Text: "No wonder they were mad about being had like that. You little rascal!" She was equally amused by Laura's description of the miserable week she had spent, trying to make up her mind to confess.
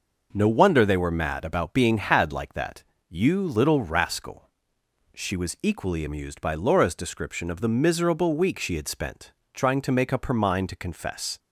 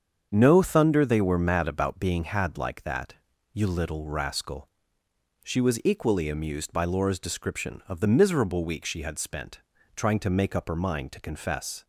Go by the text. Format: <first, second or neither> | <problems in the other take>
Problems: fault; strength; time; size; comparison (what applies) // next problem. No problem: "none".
first | starts louder than the rest; strong; until 1.3 s; 7.5 dB // says "thunder" for "wonder"; at 0.6 s